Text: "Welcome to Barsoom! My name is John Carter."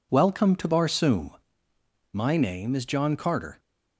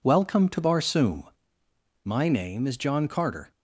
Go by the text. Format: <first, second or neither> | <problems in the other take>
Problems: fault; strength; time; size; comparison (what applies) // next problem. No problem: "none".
neither | none